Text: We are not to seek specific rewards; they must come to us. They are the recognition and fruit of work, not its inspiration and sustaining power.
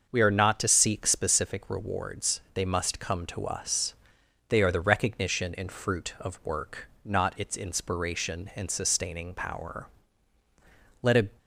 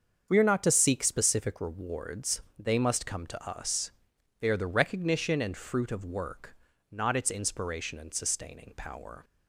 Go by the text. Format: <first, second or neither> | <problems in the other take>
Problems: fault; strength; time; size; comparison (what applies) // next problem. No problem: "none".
second | starts louder than the rest; until 1.1 s; 6.5 dB; strong in the second // goes on to say "Let a"; slight; from 11.0 s on; 0.36 s long